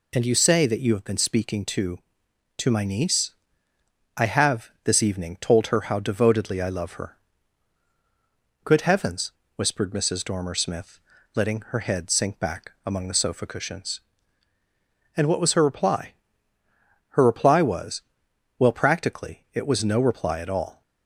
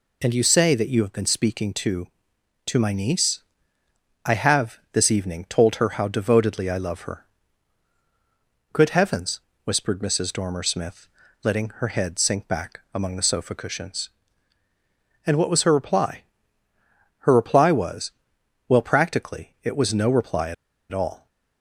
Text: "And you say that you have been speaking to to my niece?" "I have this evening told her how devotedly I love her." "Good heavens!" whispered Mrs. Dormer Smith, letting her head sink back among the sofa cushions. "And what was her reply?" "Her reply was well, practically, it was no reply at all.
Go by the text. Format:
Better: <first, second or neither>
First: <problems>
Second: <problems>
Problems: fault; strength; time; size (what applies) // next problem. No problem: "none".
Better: first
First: pauses between "was" and "well"; noticeable; at 18.0 s; 0.56 s long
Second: pauses between "was" and "well"; noticeable; at 18.1 s; 0.56 s long // pauses between "at" and "all"; at 20.5 s; 0.36 s long